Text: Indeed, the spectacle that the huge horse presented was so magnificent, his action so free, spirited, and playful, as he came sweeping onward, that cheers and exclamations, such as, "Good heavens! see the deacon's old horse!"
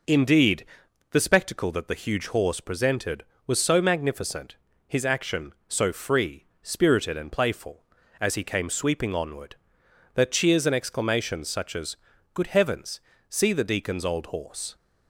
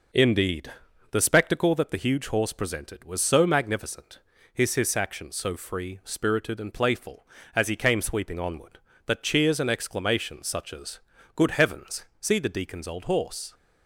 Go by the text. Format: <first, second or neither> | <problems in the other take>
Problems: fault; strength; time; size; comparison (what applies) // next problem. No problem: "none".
first | says "his" twice; at 4.7 s